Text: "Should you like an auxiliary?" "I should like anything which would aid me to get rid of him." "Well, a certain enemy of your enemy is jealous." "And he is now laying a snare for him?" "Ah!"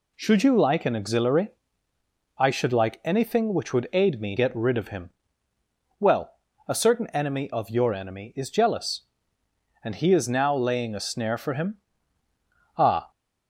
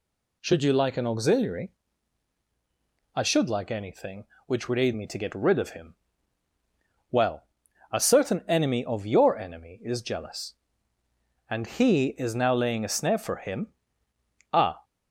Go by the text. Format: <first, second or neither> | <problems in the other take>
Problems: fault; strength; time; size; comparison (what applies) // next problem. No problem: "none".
second | skips "to"; at 4.3 s